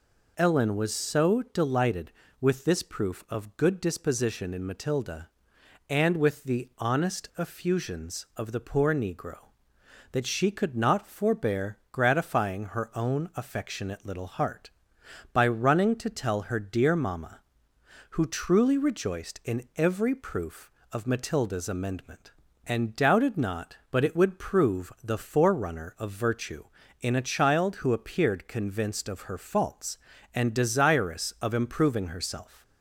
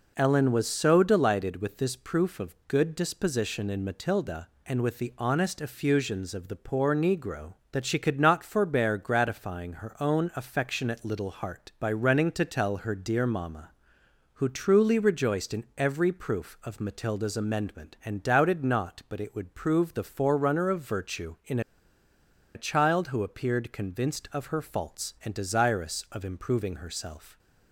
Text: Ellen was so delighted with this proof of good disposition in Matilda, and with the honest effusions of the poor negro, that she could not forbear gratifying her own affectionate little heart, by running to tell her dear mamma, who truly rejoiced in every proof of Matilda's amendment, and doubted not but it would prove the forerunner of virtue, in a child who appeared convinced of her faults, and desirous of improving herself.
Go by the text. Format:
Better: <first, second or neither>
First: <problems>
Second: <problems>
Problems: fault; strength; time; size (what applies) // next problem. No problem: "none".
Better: first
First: none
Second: pauses between "in" and "a"; noticeable; at 21.6 s; 0.94 s long